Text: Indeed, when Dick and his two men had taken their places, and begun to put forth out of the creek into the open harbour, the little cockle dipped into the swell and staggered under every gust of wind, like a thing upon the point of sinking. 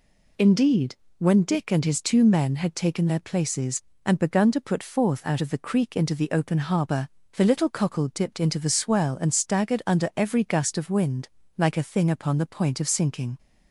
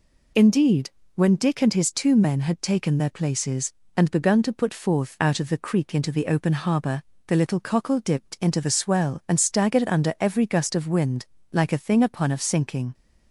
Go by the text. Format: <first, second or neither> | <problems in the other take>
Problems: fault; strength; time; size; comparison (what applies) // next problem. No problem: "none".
first | skips "the point"; at 12.3 s